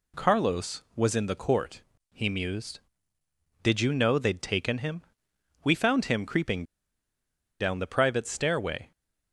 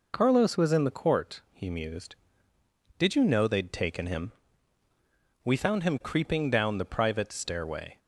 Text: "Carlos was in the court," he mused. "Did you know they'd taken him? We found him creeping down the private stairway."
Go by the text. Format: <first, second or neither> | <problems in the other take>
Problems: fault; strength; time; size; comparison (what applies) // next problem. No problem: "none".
second | pauses between "creeping" and "down"; noticeable; at 6.6 s; 0.97 s long